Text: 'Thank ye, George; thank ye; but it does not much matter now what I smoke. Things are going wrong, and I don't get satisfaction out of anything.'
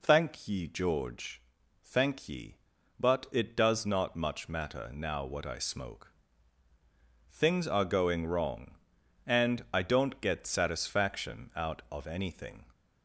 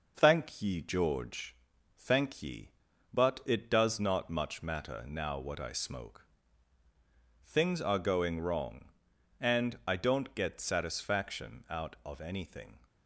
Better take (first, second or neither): first